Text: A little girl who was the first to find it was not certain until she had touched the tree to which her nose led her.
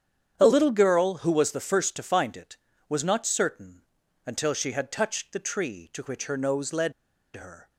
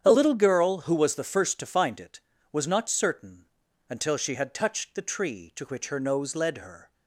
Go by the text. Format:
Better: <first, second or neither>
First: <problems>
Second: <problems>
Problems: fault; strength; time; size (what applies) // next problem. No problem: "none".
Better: second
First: starts louder than the rest; strong; until 1.3 s; 8.5 dB // pauses between "certain" and "until"; at 3.8 s; 0.42 s long // pauses between "led" and "her"; at 6.9 s; 0.43 s long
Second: starts louder than the rest; strong; until 1.0 s; 8.5 dB // pauses between "certain" and "until"; at 3.4 s; 0.42 s long